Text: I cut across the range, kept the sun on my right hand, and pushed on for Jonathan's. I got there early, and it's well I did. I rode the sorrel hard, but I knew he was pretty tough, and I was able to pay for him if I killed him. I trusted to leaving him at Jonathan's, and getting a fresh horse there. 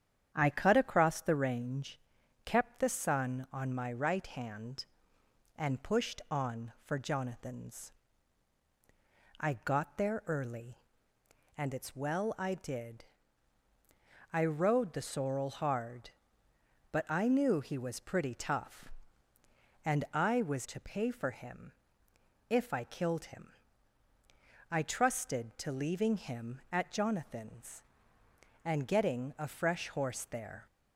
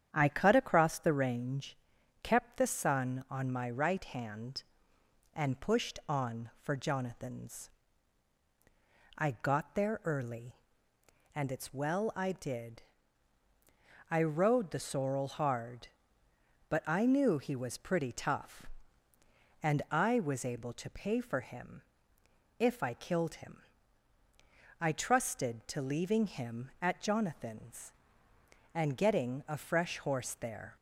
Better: second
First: starts louder than the rest; strong; until 1.3 s; 9 dB // skips "able"; at 20.6 s // pauses between "him" and "if"; noticeable; at 21.7 s; 0.76 s long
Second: starts louder than the rest; strong; until 1.1 s; 9 dB // pauses between "him" and "if"; noticeable; at 21.8 s; 0.76 s long

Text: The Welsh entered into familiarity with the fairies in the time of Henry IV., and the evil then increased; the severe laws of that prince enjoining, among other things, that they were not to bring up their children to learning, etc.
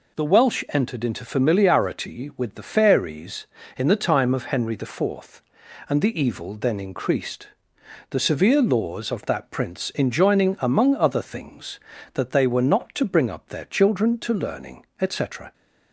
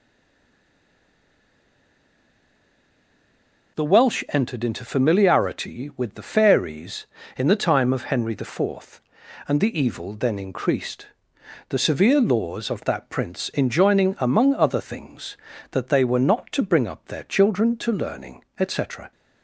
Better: first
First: none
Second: stays silent before the first word; strong; until 3.7 s; 3.7 s long

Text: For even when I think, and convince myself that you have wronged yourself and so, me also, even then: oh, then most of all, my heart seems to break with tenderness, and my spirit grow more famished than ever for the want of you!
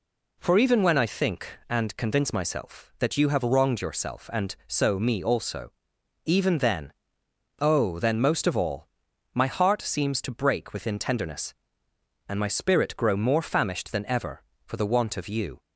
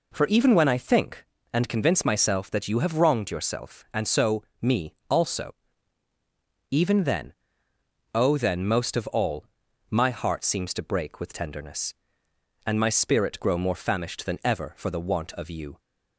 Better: second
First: says "within" for "with"; at 10.7 s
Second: none

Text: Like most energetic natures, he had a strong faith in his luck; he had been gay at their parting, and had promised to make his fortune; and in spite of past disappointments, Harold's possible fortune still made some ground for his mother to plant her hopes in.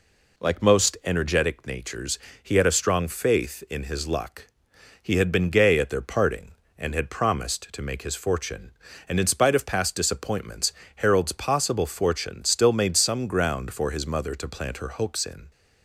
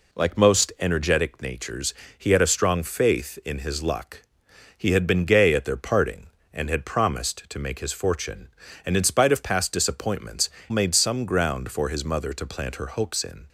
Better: first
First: none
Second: skips "Harold's possible fortune still"; at 10.5 s

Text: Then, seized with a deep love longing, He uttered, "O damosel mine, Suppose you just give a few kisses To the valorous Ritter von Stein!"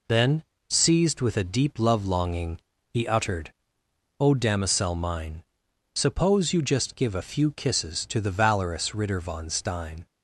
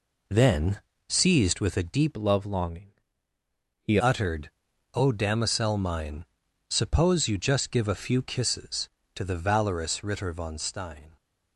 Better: first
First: none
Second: changes voice from "love" to "He"; from 2.1 to 3.9 s; 1.8 s long

